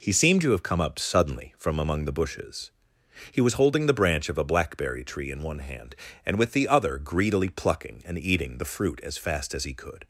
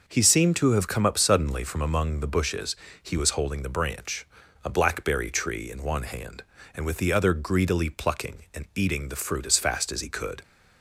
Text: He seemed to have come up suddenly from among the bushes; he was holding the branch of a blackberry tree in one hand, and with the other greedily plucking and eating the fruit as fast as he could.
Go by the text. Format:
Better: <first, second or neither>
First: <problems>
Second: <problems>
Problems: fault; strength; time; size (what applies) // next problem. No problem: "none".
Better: first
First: none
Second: skips "of"; at 4.4 s